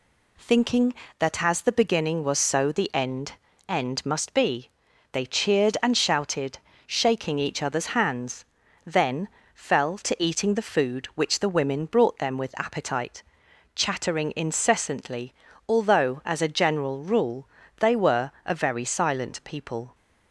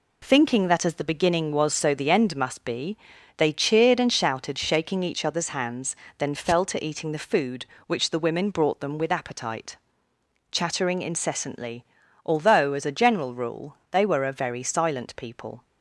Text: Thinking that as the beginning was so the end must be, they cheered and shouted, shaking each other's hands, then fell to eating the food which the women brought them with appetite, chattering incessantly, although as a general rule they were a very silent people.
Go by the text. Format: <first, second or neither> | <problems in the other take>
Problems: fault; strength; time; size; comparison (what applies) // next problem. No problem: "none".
second | says "end" twice; at 3.6 s // pauses between "then" and "fell"; slight; at 9.2 s; 0.26 s long // pauses between "rule" and "they"; slight; at 17.4 s; 0.32 s long; slight in the second